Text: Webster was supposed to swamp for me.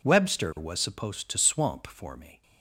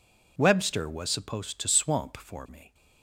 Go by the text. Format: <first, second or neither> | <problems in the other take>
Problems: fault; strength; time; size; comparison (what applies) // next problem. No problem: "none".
neither | none